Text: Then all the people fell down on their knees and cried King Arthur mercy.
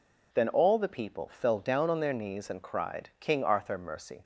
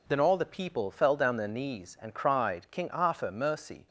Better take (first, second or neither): first